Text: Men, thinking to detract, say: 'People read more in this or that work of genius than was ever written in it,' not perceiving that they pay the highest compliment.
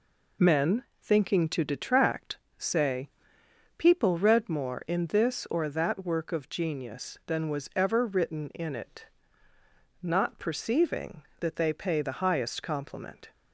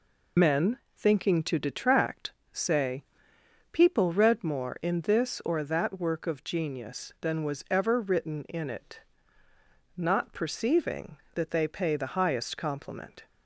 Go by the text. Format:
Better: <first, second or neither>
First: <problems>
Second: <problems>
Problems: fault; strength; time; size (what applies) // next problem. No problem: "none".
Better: first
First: none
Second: loses the start of "Men"; at 0.3 s; 35 ms